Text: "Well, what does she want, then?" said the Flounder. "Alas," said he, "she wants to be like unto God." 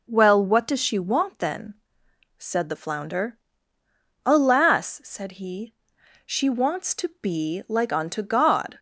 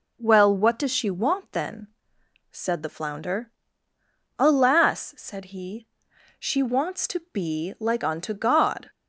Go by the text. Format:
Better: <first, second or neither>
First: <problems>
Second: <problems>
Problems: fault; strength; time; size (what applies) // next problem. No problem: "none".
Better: neither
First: none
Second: none